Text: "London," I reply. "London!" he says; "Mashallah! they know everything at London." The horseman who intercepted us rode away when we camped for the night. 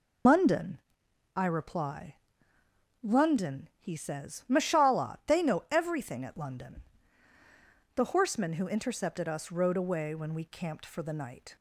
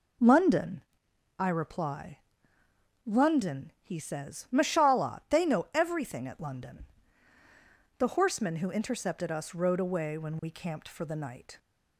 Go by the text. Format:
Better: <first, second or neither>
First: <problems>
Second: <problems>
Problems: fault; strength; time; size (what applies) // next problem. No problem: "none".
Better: second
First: loses the start of "London"; at 0.2 s; 75 ms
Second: none